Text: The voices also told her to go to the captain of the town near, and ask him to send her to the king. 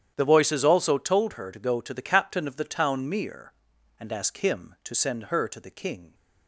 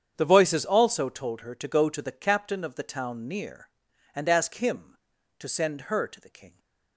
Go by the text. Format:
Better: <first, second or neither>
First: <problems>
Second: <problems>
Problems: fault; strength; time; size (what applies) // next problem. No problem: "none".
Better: second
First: starts louder than the rest; strong; until 1.1 s; 10 dB // says "mere" for "near"; at 3.0 s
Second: starts louder than the rest; strong; until 1.1 s; 8 dB